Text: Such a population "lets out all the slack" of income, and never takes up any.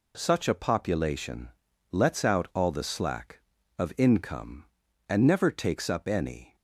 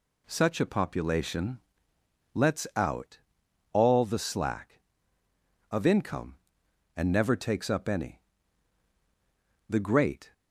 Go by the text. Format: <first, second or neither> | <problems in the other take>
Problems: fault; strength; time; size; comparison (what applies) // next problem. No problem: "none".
first | pauses between "population" and "lets"; noticeable; at 1.6 s; 0.72 s long; also in the first // pauses between "out" and "all"; noticeable; at 3.1 s; 0.54 s long // goes on to say "The great"; noticeable; from 9.6 s on; 0.64 s long